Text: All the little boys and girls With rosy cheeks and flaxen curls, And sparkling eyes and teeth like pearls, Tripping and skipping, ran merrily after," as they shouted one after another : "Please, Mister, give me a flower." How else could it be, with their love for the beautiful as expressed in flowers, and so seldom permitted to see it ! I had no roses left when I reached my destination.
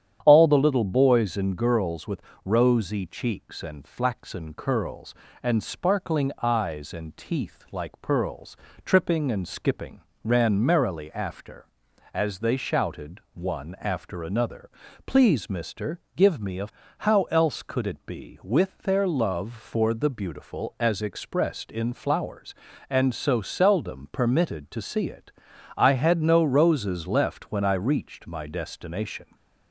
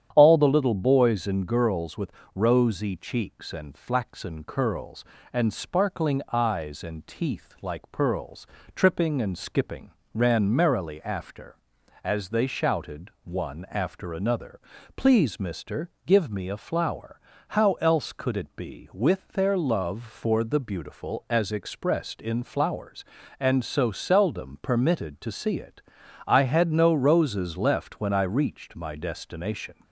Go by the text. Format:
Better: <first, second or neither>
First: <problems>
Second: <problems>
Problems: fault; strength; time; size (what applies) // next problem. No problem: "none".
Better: second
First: starts louder than the rest; strong; until 1.2 s; 9.5 dB // pauses between "With" and "rosy"; slight; at 2.2 s; 0.24 s long // skips "flower"; at 16.8 s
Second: starts louder than the rest; strong; until 1.1 s; 9.5 dB // pauses between "With" and "rosy"; slight; at 2.1 s; 0.24 s long